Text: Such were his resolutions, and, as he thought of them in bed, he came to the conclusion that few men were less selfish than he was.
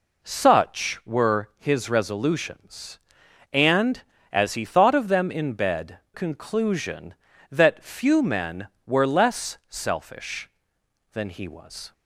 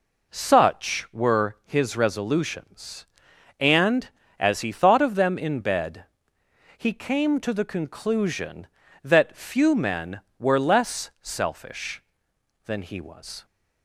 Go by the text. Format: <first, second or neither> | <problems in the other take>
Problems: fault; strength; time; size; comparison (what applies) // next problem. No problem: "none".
second | skips "he came to the"; at 6.0 s